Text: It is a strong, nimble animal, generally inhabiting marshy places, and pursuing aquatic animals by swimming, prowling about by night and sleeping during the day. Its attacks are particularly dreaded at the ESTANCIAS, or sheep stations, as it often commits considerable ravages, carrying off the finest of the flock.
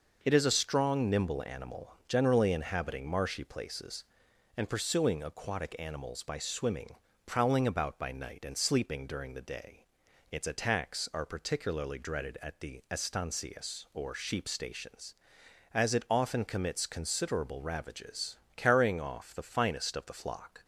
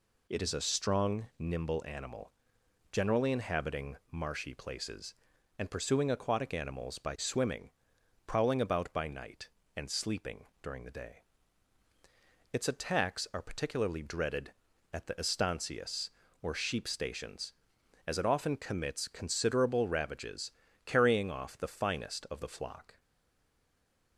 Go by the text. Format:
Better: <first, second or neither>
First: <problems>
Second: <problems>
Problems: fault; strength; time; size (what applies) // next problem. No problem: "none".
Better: first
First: none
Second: pauses between "inhabiting" and "marshy"; slight; at 3.9 s; 0.16 s long // pauses between "sleeping" and "during"; slight; at 10.4 s; 0.16 s long // stays silent after the last word; noticeable; from 22.9 s on; 1.2 s long